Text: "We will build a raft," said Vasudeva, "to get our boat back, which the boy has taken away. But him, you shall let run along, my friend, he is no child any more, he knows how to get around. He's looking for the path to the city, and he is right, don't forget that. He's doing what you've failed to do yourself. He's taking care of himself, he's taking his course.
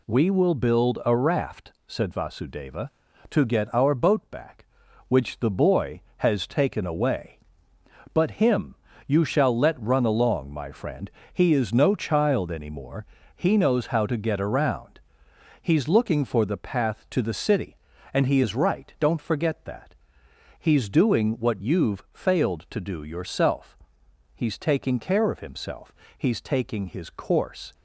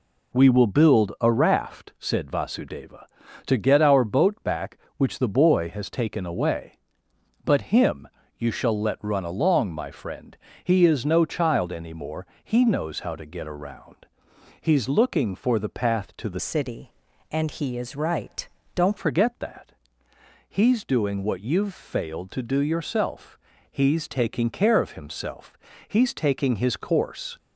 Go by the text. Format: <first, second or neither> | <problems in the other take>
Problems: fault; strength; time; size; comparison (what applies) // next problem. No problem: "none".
first | changes voice from "city" to "don't"; from 16.3 to 18.9 s; 2.6 s long